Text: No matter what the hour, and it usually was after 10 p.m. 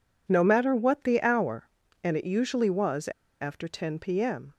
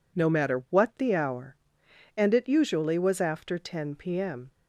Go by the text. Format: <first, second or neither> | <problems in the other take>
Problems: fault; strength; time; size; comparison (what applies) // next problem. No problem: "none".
second | pauses between "was" and "after"; slight; at 3.0 s; 0.33 s long